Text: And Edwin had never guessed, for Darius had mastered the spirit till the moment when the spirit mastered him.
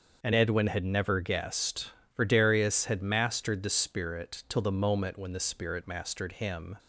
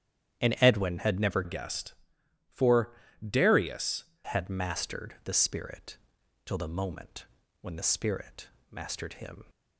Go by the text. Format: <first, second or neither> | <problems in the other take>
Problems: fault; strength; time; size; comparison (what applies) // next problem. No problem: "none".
first | starts louder than the rest; strong; until 1.4 s; 10 dB; noticeable in the first // changes voice from "guessed" to "Darius"; from 1.4 to 4.0 s; 2.6 s long // pauses between "for" and "Darius"; slight; at 2.9 s; 0.32 s long // pauses between "spirit" and "till"; noticeable; at 5.9 s; 0.48 s long // pauses between "moment" and "when"; slight; at 7.2 s; 0.36 s long // pauses between "spirit" and "mastered"; slight; at 8.4 s; 0.22 s long